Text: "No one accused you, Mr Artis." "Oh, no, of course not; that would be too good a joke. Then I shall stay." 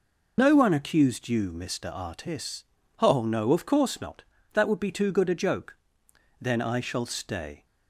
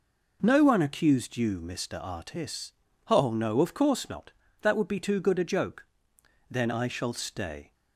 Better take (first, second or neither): second